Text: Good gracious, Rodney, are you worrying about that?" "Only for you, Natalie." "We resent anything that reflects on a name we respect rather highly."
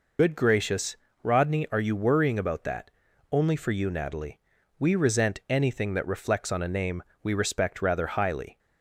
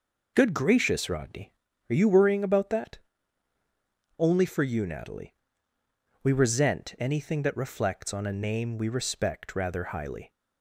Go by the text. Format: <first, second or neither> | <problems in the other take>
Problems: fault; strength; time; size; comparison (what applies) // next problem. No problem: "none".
second | loses the start of "Good"; at 0.1 s; 35 ms // pauses between "name" and "we"; slight; at 7.0 s; 0.18 s long